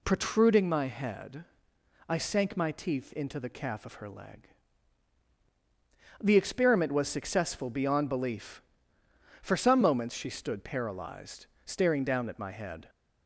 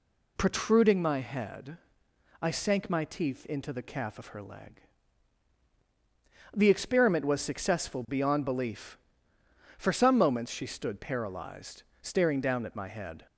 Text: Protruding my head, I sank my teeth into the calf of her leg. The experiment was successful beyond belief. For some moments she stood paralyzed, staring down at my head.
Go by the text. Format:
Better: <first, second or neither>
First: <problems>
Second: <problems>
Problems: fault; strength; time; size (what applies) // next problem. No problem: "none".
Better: neither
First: none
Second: none